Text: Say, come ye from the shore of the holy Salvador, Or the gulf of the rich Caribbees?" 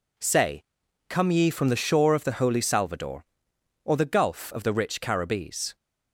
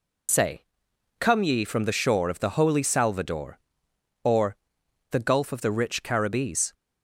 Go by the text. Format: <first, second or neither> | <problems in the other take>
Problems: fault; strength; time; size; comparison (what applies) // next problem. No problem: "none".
first | loses the start of "Say"; at 0.2 s; 80 ms // pauses between "Or" and "the"; noticeable; at 4.5 s; 0.54 s long